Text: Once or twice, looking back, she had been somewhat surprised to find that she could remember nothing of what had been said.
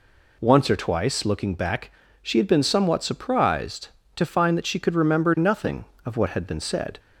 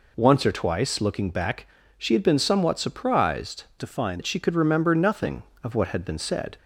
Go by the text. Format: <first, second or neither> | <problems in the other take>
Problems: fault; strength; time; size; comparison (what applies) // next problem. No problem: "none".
first | changes voice from "to" to "find"; from 3.8 to 4.2 s; 0.4 s long